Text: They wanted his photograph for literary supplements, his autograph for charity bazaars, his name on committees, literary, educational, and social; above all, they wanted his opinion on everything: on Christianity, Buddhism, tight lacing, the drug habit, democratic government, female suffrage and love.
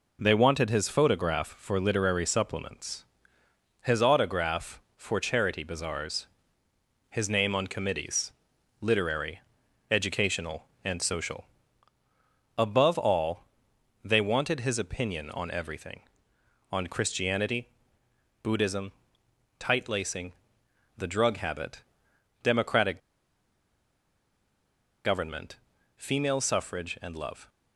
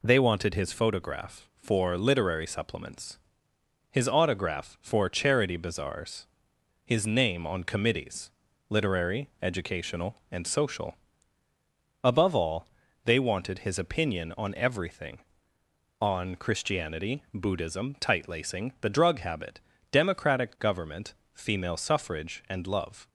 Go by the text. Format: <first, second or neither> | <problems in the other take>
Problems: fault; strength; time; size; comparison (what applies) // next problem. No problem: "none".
second | pauses between "democratic" and "government"; strong; at 22.9 s; 2.0 s long